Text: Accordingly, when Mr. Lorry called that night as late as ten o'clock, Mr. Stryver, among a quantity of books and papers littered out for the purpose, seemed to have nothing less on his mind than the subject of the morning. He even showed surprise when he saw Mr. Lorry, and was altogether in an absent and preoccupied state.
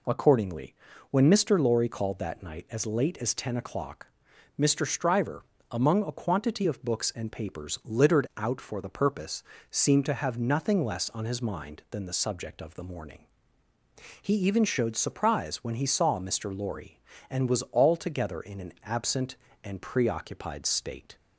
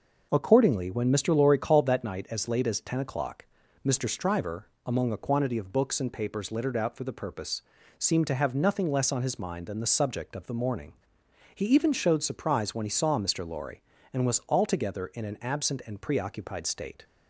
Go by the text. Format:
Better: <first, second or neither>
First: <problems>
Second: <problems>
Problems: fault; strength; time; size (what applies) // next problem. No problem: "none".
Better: neither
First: none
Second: none